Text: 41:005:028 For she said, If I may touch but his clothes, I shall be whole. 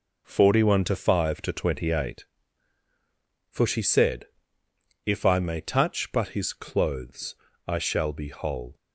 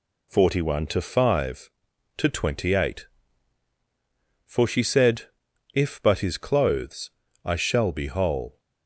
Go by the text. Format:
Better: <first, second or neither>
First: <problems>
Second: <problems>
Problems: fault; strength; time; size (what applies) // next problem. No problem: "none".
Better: first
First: none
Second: skips "I may touch"; at 6.0 s